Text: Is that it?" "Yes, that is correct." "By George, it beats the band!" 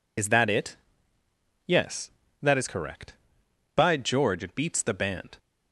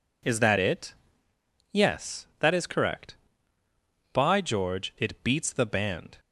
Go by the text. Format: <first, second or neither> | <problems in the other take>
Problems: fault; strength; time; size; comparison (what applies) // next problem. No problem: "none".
second | loses the start of "Is"; at 0.1 s; 55 ms